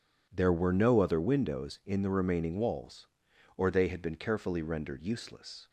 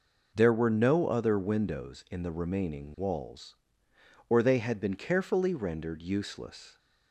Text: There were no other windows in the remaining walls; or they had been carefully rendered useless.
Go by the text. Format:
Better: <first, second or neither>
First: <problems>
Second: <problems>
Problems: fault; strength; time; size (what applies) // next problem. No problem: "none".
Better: neither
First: none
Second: none